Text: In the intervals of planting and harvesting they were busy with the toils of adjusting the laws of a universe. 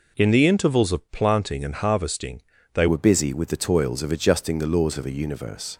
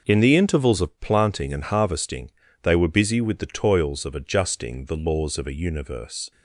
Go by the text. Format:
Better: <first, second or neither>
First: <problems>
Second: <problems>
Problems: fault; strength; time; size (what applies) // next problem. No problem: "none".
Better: second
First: pauses between "harvesting" and "they"; slight; at 2.4 s; 0.32 s long // changes voice at "were"; from 2.8 s on; 2.9 s long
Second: pauses between "harvesting" and "they"; slight; at 2.3 s; 0.32 s long